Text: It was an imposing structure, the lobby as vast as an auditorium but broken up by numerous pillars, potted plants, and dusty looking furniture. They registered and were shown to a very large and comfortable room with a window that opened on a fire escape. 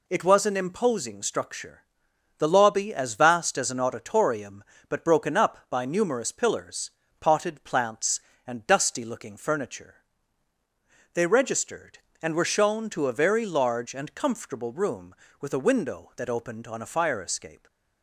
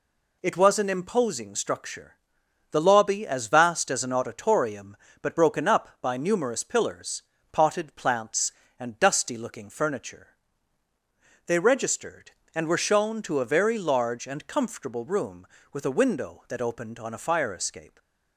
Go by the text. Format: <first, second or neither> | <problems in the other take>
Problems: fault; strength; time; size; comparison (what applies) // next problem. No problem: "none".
neither | none